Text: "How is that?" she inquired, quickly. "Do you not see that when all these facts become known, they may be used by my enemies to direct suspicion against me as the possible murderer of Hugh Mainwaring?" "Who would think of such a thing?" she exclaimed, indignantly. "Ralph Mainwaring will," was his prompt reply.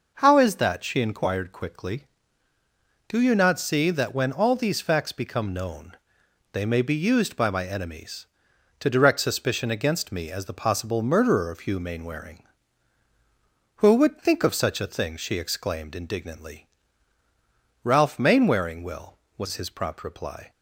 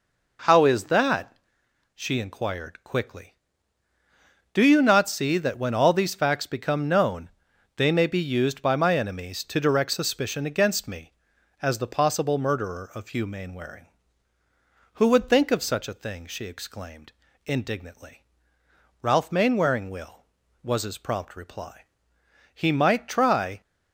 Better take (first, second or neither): first